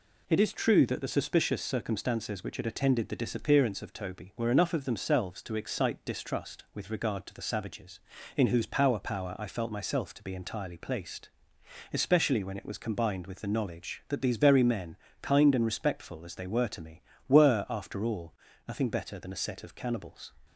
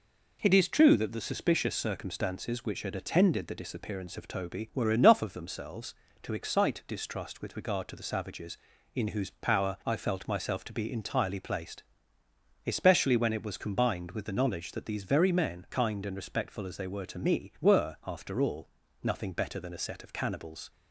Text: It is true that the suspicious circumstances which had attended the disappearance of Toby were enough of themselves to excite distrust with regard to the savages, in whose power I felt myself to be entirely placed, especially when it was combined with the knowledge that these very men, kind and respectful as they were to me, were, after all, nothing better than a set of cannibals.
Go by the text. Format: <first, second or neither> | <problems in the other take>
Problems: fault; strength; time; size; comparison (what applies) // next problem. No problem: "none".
second | says "power" twice; at 8.9 s